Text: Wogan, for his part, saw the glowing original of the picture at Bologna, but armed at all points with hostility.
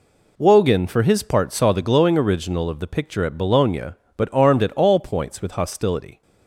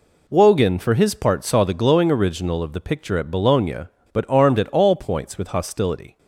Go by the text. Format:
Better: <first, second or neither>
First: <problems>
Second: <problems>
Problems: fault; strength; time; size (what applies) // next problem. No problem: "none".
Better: neither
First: none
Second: none